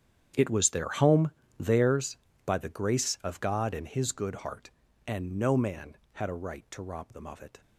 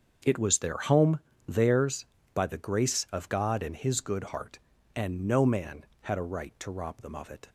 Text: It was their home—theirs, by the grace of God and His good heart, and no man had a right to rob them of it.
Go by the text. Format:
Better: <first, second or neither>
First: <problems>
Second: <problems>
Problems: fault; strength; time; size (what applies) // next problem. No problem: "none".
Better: second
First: gets quieter; strong; throughout; 17 dB // starts louder than the rest; strong; until 1.6 s; 9 dB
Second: starts louder than the rest; until 1.5 s; 6.5 dB